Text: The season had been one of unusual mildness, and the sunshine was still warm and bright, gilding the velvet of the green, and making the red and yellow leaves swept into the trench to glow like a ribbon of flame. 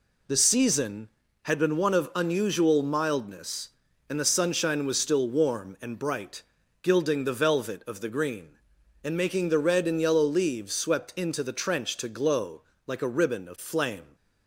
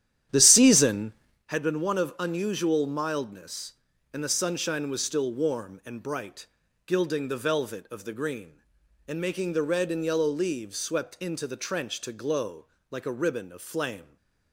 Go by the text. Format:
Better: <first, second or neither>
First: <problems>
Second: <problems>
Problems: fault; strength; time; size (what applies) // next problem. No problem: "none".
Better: first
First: pauses between "glow" and "like"; slight; at 12.6 s; 0.26 s long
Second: starts louder than the rest; strong; until 1.4 s; 11 dB // pauses between "glow" and "like"; slight; at 12.6 s; 0.26 s long